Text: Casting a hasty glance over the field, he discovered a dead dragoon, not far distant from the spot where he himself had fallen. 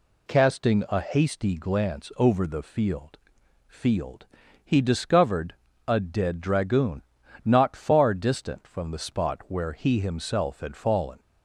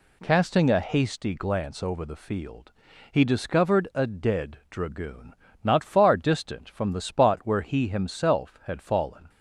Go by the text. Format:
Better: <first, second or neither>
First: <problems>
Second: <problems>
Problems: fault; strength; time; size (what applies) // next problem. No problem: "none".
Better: second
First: says "field" twice; at 3.6 s // pauses between "discovered" and "a"; slight; at 5.5 s; 0.34 s long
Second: none